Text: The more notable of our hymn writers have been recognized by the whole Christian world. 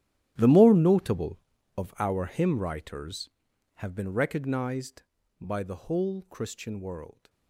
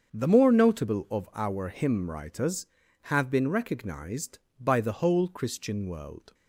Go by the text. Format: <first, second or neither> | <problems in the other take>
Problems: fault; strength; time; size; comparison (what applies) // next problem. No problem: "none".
second | gets quieter; strong; throughout; 18 dB // starts louder than the rest; strong; until 1.3 s; 12.5 dB; strong in the second